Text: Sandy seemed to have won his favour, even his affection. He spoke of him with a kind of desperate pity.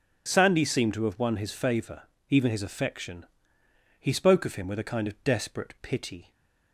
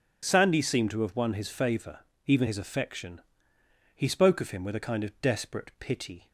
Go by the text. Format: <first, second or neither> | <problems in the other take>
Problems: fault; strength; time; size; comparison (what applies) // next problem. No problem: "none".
neither | none